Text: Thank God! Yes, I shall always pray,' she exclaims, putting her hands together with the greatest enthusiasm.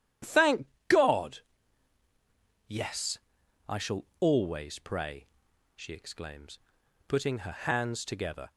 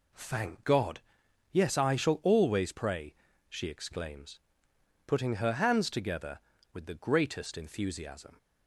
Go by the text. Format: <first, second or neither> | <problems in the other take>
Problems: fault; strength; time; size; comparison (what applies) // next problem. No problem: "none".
second | starts louder than the rest; strong; until 2.7 s; 10.5 dB // pauses between "Thank" and "God"; slight; at 0.6 s; 0.20 s long // pauses between "shall" and "always"; slight; at 4.0 s; 0.16 s long // stops before "with the greatest enthusiasm"; at 8.5 s